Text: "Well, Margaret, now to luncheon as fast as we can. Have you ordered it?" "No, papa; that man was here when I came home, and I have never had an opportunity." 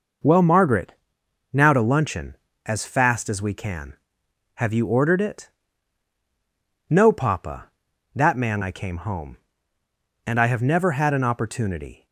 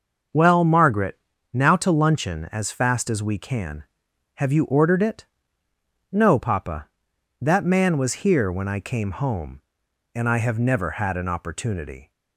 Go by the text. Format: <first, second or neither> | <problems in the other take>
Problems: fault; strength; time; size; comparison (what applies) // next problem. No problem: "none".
second | skips "was here when"; at 8.6 s